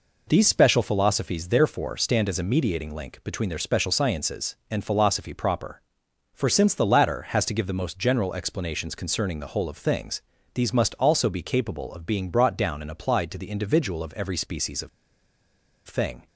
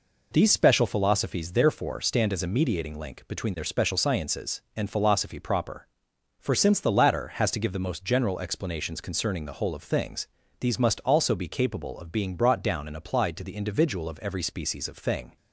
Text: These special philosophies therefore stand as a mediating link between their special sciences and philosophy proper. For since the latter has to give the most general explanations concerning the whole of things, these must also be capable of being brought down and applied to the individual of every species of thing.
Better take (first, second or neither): second